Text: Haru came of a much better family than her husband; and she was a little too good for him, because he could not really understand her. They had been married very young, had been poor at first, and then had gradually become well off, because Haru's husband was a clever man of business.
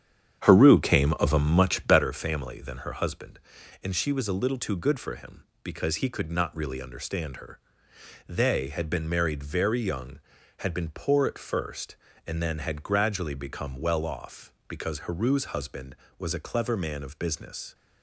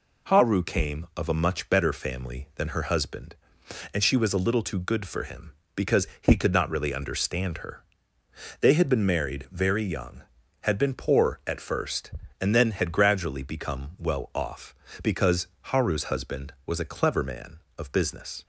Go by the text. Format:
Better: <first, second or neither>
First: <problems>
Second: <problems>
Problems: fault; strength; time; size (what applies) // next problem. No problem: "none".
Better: second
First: starts louder than the rest; strong; until 2.0 s; 8.5 dB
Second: none